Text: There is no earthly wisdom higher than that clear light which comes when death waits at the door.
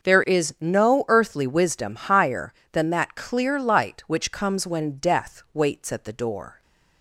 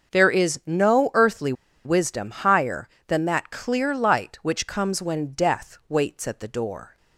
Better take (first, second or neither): first